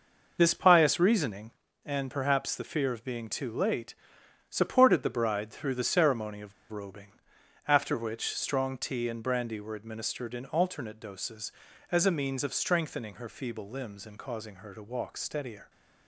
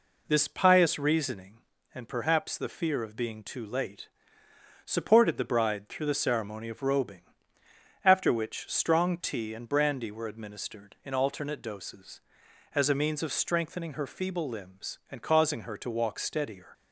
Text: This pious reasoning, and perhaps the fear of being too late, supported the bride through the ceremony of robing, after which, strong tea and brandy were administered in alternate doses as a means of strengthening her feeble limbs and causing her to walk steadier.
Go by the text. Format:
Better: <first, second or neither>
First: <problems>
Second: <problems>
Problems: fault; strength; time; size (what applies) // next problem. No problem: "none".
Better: second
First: pauses between "of" and "robing"; slight; at 6.5 s; 0.19 s long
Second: none